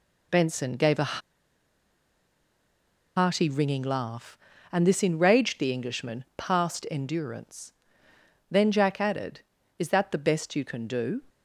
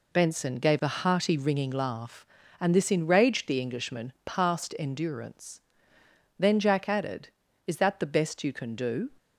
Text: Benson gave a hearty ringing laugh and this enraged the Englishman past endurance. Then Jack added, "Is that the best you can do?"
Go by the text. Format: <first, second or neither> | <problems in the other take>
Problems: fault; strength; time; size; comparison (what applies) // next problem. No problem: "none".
second | pauses between "a" and "hearty"; strong; at 1.1 s; 1.9 s long